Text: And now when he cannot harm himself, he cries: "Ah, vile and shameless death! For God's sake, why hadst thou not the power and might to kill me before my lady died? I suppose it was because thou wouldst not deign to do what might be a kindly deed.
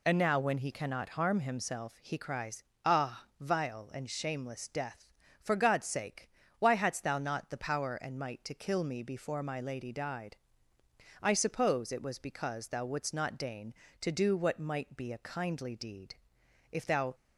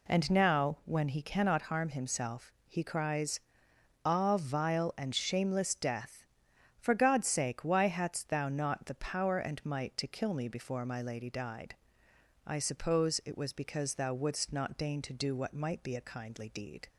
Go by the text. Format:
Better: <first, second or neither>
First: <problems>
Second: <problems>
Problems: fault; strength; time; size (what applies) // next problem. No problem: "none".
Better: second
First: goes on to say "If thou"; slight; from 16.7 s on; 0.42 s long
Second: none